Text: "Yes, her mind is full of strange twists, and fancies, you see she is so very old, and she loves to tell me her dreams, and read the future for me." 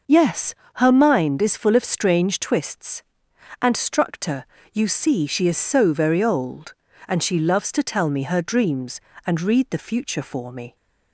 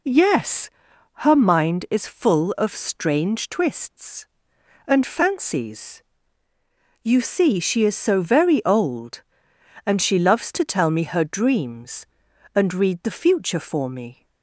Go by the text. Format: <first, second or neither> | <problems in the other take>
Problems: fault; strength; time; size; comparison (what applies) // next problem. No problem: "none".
second | says "structor" for "fancies"; at 3.7 s